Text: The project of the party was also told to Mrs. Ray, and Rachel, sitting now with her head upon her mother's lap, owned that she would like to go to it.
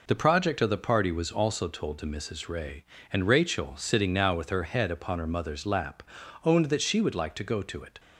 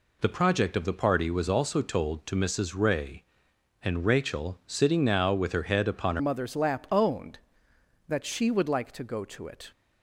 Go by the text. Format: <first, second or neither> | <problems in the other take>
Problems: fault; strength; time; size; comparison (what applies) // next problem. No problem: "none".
first | changes voice at "mother's"; from 6.1 s on; 3.6 s long